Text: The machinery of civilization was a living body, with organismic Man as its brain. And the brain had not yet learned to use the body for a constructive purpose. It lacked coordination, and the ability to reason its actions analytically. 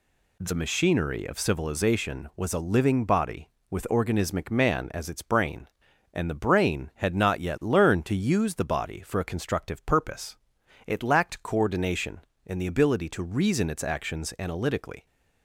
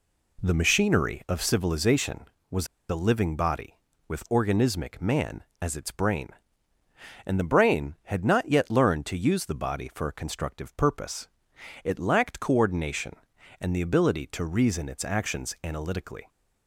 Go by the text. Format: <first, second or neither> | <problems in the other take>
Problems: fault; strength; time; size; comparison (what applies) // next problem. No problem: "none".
first | pauses between "was" and "a"; slight; at 2.6 s; 0.23 s long